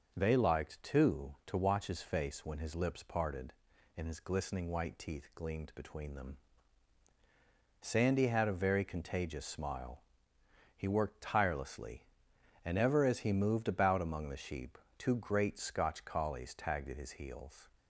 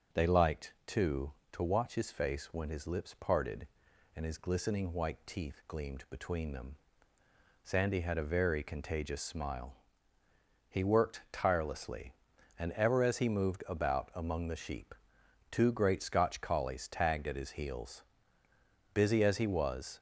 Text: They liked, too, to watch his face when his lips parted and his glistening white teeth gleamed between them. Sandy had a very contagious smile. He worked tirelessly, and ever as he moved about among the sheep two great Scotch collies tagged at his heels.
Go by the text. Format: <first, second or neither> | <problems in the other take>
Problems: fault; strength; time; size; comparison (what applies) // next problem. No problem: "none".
first | starts louder than the rest; until 1.2 s; 6 dB; noticeable in the first // pauses between "sheep" and "two"; noticeable; at 14.9 s; 0.58 s long; slight in the first // goes on to say "Busy as he was"; noticeable; from 18.9 s on; 1.0 s long